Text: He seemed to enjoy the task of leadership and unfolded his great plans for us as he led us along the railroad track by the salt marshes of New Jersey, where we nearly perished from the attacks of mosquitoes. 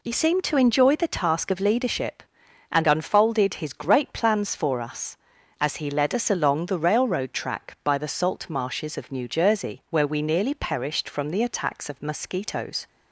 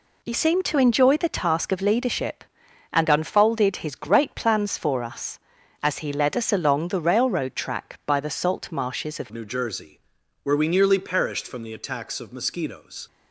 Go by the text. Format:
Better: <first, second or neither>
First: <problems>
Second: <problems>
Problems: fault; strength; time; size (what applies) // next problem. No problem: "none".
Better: first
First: none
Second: changes voice at "New"; from 9.3 s on; 3.7 s long